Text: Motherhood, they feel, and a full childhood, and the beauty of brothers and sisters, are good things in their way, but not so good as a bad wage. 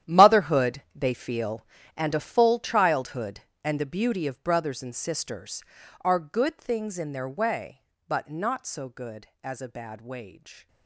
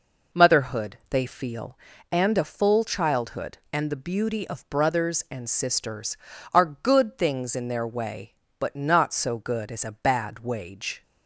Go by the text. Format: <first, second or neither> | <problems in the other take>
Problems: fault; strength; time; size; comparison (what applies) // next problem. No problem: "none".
second | gets quieter; strong; throughout; 15 dB